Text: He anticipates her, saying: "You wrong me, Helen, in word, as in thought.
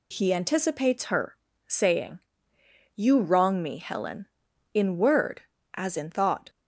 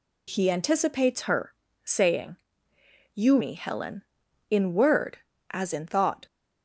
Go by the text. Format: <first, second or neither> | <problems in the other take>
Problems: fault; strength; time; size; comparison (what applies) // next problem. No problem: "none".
first | skips "wrong"; at 3.3 s